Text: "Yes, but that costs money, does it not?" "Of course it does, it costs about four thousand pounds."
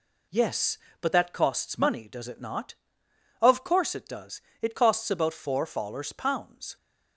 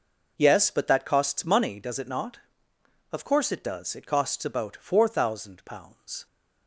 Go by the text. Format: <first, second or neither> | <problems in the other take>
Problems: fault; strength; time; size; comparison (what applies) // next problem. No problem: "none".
second | says "fallers" for "thousand"; at 5.6 s